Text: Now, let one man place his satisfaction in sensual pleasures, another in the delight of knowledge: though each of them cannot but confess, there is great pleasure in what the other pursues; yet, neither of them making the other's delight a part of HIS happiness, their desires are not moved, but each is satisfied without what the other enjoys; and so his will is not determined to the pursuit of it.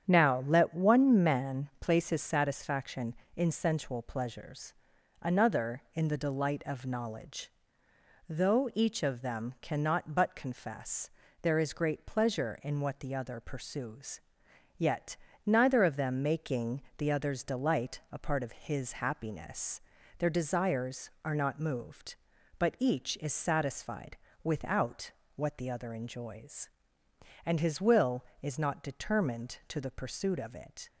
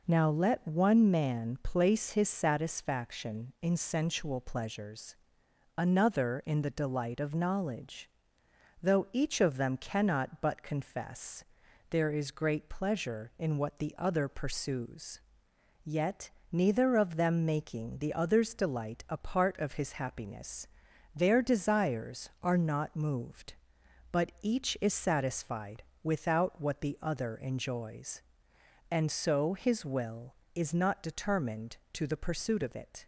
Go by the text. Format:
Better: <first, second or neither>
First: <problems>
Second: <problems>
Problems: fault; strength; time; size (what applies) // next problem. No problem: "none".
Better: second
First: starts louder than the rest; strong; until 1.0 s; 8.5 dB // pauses between "making" and "the"; slight; at 16.8 s; 0.16 s long // pauses between "satisfied" and "without"; slight; at 24.1 s; 0.28 s long // pauses between "without" and "what"; slight; at 25.1 s; 0.24 s long // skips "so"; at 27.6 s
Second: pauses between "satisfied" and "without"; slight; at 25.8 s; 0.22 s long